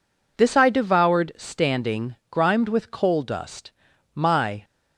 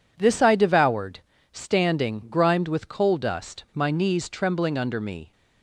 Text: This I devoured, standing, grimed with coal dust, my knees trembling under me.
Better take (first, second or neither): second